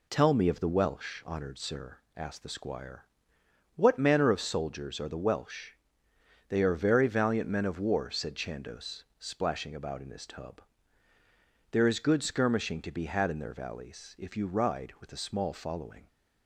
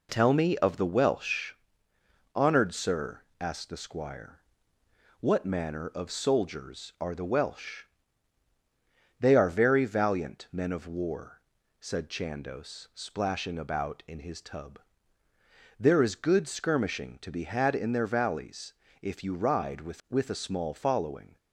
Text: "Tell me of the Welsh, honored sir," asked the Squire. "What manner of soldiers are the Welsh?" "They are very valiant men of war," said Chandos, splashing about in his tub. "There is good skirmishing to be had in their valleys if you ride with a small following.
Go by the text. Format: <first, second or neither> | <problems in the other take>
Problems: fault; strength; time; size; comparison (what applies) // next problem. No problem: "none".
first | pauses between "valleys" and "if"; slight; at 18.7 s; 0.30 s long // says "with" twice; at 20.1 s